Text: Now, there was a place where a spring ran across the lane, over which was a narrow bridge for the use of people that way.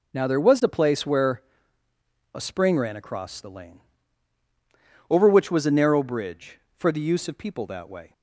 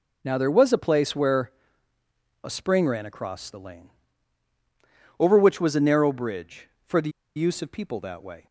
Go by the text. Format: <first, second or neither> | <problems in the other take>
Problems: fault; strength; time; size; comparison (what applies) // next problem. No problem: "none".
first | pauses between "where" and "a"; noticeable; at 1.4 s; 0.94 s long; noticeable in the first // pauses between "the" and "use"; slight; at 7.0 s; 0.26 s long